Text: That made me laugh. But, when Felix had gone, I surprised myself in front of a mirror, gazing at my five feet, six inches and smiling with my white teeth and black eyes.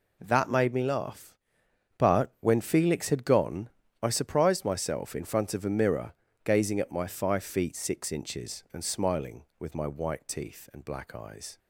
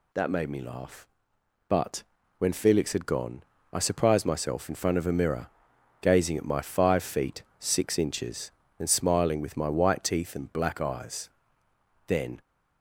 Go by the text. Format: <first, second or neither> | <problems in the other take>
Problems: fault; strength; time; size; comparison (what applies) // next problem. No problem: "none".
first | goes on to say "Then"; slight; from 12.0 s on; 0.34 s long